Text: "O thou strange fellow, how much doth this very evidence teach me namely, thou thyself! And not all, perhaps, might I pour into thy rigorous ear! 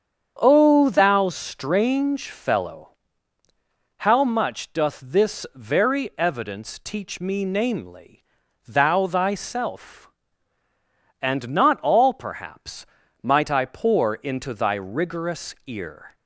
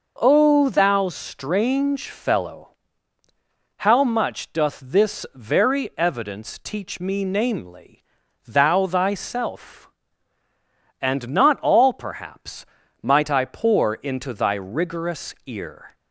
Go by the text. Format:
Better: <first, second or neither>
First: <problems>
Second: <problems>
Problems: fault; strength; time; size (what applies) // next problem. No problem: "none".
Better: second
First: starts louder than the rest; strong; until 2.0 s; 8 dB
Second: none